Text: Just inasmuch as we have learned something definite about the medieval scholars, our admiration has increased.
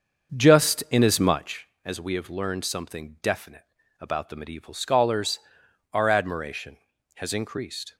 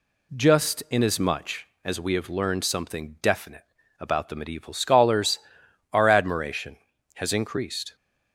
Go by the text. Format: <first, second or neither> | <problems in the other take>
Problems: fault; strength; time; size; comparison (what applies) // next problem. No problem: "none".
second | starts louder than the rest; until 1.5 s; 6.5 dB // pauses between "definite" and "about"; slight; at 3.6 s; 0.36 s long; slight in the second